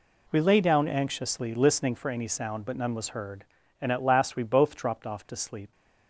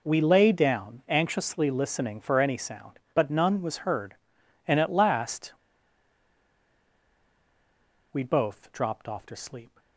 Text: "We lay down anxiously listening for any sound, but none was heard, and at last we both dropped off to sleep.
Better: first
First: none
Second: pauses between "last" and "we"; strong; at 5.5 s; 2.5 s long

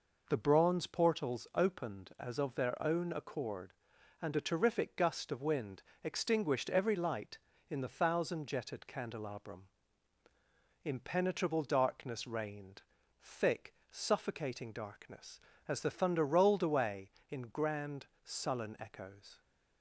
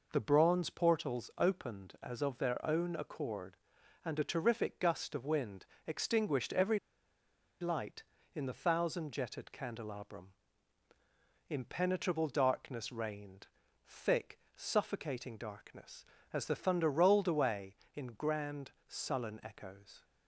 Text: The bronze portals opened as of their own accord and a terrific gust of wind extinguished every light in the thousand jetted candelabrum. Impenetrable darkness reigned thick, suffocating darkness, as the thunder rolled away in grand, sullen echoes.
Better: first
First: pauses between "wind" and "extinguished"; slight; at 5.8 s; 0.20 s long // pauses between "reigned" and "thick"; at 12.8 s; 0.42 s long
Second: pauses between "wind" and "extinguished"; slight; at 5.6 s; 0.20 s long // pauses between "every" and "light"; noticeable; at 6.7 s; 0.82 s long // pauses between "reigned" and "thick"; at 13.4 s; 0.42 s long

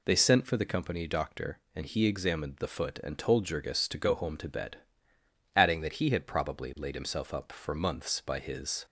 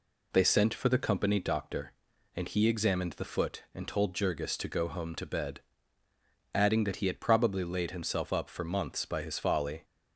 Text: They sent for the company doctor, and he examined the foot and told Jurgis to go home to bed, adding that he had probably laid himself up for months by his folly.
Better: second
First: stops before "folly"; at 8.8 s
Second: none

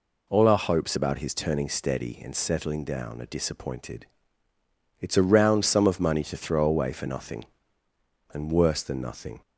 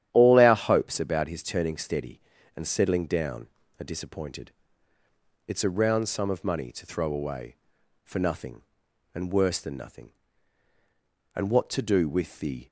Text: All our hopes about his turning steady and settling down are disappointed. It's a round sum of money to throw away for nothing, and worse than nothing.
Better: first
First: none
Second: starts louder than the rest; strong; until 1.1 s; 10.5 dB // goes on to say "And what to do with the"; from 11.3 s on; 1.3 s long

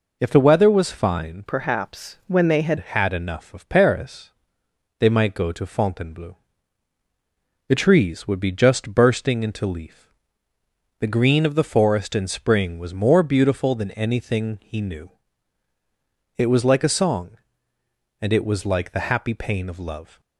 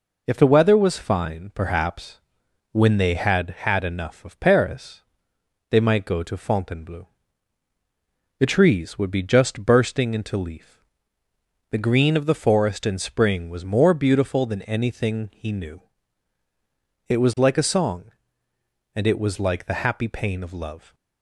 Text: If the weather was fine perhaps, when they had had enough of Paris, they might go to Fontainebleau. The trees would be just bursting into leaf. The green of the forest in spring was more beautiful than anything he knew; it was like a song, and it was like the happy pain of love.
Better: second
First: changes voice from "perhaps" to "had"; from 1.4 to 2.7 s; 1.3 s long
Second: none

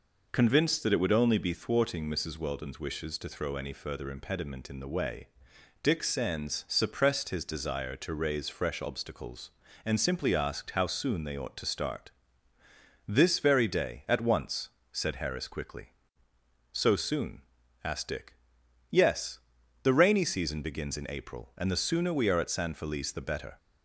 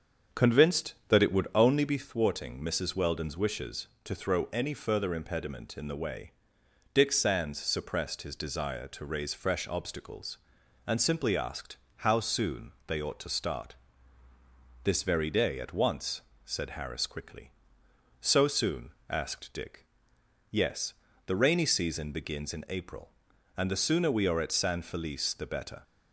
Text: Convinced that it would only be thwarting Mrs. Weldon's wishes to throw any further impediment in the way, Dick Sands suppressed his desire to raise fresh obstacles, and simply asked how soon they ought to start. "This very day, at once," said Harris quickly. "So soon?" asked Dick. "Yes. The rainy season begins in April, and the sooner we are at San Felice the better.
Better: first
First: none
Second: starts louder than the rest; until 2.1 s; 7 dB // pauses between "asked" and "how"; slight; at 11.7 s; 0.22 s long // pauses between "soon" and "they"; slight; at 12.7 s; 0.16 s long

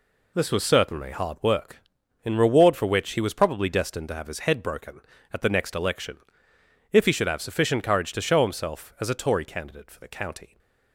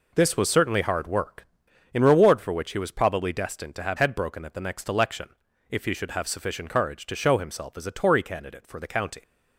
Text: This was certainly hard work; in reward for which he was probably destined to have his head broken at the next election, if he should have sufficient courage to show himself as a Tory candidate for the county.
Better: first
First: none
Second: skips "his"; at 3.9 s

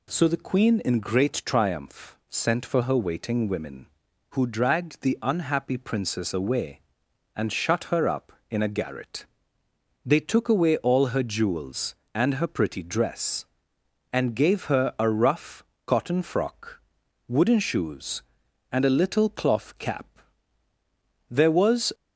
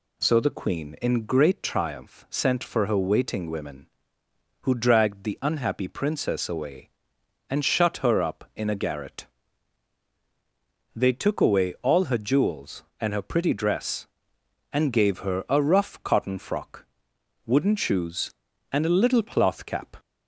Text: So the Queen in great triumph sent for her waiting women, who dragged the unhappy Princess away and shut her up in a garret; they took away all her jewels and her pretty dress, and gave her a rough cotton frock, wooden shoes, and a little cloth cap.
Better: second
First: pauses between "rough" and "cotton"; slight; at 15.6 s; 0.22 s long // goes on to say "There was"; noticeable; from 21.2 s on; 0.64 s long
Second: none

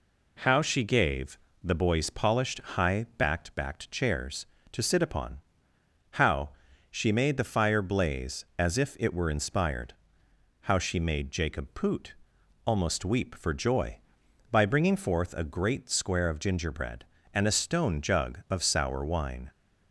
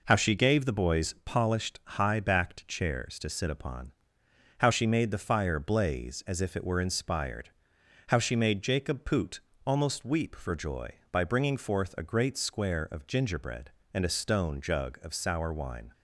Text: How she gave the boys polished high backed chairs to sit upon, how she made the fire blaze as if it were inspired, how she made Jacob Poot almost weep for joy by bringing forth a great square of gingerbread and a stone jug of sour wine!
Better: second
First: pauses between "gave" and "the"; slight; at 1.3 s; 0.24 s long // says "backed" twice; at 3.5 s // pauses between "how" and "she"; at 6.4 s; 0.42 s long // pauses between "Poot" and "almost"; noticeable; at 12.1 s; 0.54 s long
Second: pauses between "Poot" and "almost"; slight; at 9.4 s; 0.22 s long

